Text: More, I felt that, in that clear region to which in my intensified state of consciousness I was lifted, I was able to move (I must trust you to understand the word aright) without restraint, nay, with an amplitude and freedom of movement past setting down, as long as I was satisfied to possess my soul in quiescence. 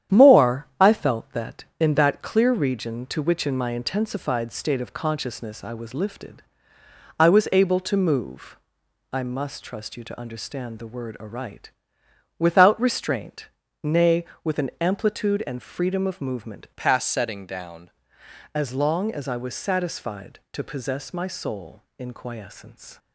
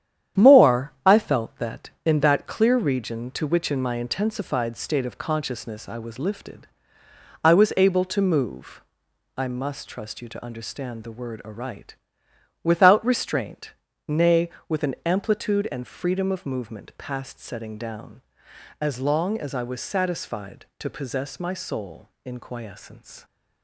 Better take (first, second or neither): second